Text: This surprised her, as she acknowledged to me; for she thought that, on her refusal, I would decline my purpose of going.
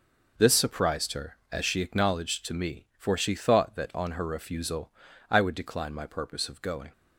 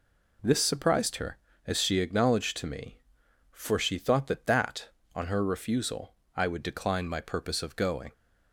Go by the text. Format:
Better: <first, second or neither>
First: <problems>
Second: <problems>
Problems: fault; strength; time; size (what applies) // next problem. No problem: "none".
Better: first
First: none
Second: says "that" twice; at 4.4 s